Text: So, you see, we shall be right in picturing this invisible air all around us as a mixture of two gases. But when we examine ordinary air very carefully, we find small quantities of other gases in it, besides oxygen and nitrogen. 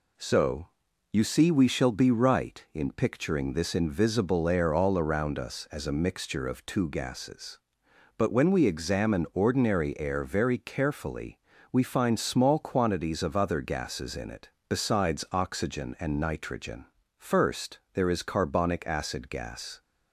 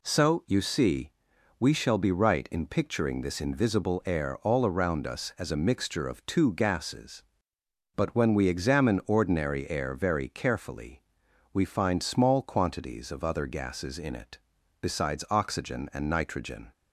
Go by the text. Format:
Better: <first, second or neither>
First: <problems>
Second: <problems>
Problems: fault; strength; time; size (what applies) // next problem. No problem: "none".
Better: second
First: goes on to say "First there is carbonic acid gas"; strong; from 17.1 s on; 2.6 s long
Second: none